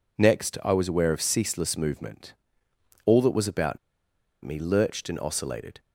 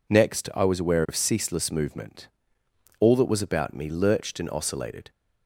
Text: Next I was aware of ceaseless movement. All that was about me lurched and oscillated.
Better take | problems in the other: second | pauses between "about" and "me"; noticeable; at 3.7 s; 0.65 s long

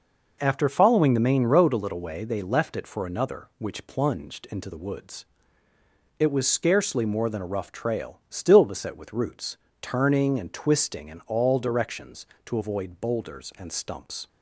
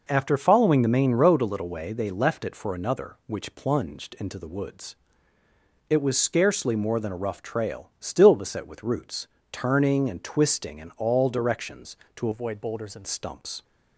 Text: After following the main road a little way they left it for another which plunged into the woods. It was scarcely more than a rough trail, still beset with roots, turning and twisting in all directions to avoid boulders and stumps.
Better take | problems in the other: first | changes voice from "avoid" to "and"; from 12.3 to 13.0 s; 0.7 s long

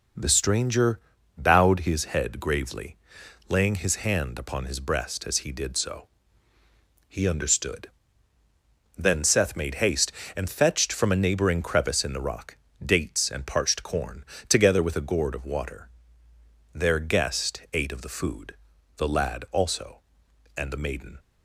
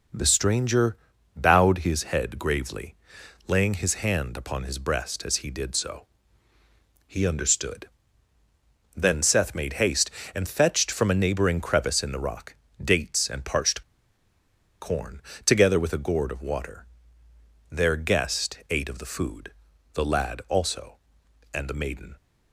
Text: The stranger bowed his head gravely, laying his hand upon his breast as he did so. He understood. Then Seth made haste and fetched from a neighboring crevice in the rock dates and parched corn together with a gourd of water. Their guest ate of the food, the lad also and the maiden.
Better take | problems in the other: first | pauses between "stranger" and "bowed"; at 0.9 s; 0.40 s long; also in the first // pauses between "rock" and "dates"; slight; at 12.5 s; 0.30 s long; slight in the first // pauses between "parched" and "corn"; at 13.8 s; 0.99 s long // pauses between "corn" and "together"; slight; at 15.2 s; 0.24 s long; slight in the first

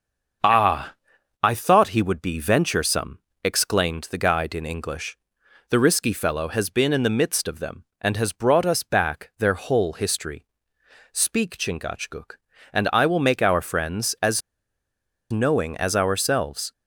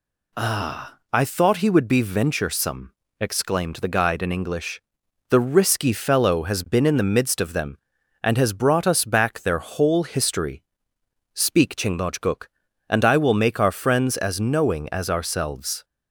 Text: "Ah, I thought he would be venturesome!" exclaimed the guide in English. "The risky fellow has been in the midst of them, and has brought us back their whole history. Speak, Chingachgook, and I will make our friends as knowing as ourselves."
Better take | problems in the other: second | starts louder than the rest; until 1.9 s; 6.5 dB // pauses between "as" and "knowing"; noticeable; at 14.4 s; 0.90 s long

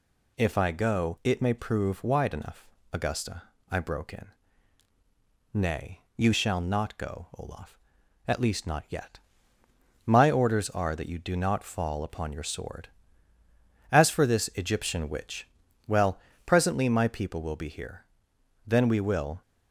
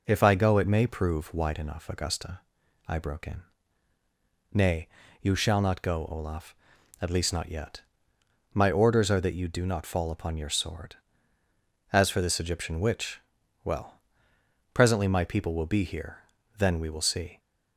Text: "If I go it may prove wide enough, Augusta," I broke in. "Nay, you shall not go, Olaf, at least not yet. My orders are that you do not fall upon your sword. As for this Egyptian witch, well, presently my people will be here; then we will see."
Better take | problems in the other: second | stops before "see"; at 19.4 s

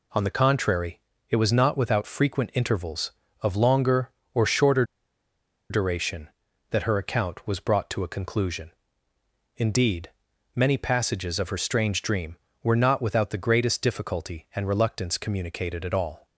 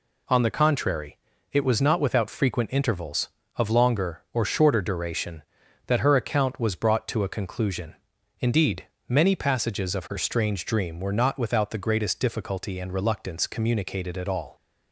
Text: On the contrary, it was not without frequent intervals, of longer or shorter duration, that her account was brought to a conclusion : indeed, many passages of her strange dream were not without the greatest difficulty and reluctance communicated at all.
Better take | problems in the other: second | pauses between "shorter" and "duration"; noticeable; at 4.8 s; 0.86 s long

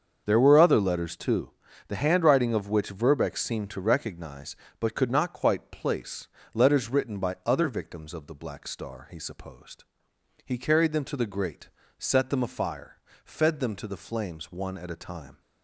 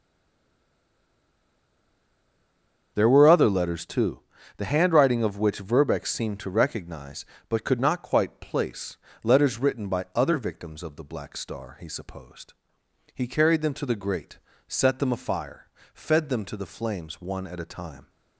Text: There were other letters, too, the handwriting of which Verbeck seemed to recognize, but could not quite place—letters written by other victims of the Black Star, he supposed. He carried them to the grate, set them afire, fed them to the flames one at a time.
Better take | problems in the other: first | stays silent before the first word; strong; until 2.9 s; 2.9 s long // starts louder than the rest; until 3.9 s; 6.5 dB; also in the first

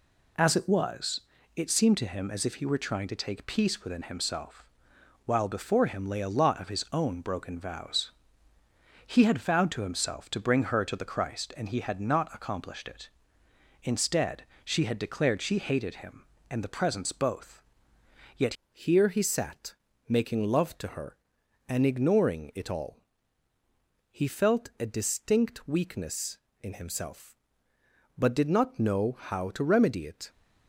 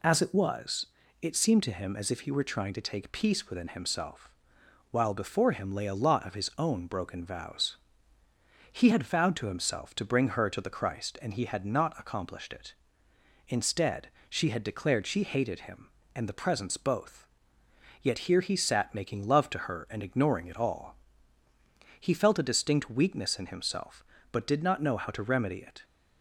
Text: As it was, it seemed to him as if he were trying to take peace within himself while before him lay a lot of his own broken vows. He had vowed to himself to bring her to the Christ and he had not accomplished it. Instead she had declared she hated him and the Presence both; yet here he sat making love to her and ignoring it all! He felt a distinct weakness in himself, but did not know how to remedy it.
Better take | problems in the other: second | pauses between "himself" and "while"; noticeable; at 4.6 s; 0.62 s long; noticeable in the second // pauses between "Instead" and "she"; slight; at 14.4 s; 0.20 s long; slight in the second // changes voice at "here"; from 18.7 s on; 11.5 s long // pauses between "sat" and "making"; slight; at 19.7 s; 0.34 s long

